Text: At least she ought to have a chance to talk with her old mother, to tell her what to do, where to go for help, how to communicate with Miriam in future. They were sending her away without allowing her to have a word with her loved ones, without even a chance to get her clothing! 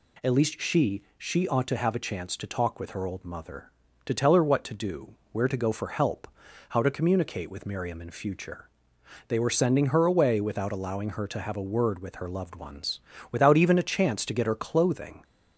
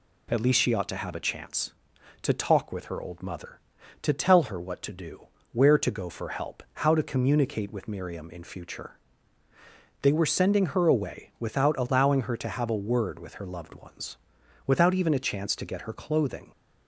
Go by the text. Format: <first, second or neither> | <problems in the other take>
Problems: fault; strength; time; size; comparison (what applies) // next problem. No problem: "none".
second | says "she" twice; at 1.1 s